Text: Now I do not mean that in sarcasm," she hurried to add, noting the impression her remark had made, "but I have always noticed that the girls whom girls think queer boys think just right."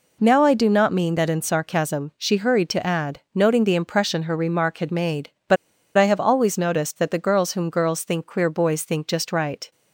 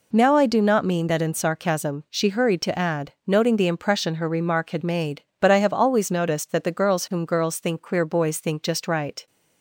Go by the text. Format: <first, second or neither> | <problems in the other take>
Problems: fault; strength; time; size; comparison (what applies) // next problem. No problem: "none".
second | pauses between "but" and "I"; at 5.5 s; 0.40 s long